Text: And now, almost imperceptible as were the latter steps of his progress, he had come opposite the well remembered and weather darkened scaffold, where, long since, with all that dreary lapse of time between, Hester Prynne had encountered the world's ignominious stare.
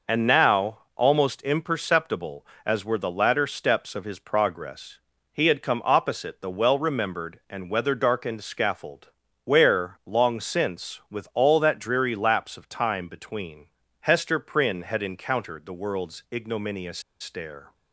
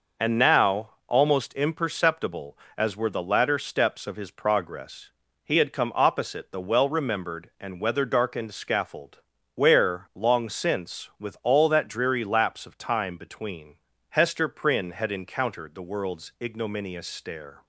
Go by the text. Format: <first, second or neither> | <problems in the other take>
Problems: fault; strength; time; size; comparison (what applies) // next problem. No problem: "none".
second | pauses between "ignominious" and "stare"; slight; at 16.9 s; 0.20 s long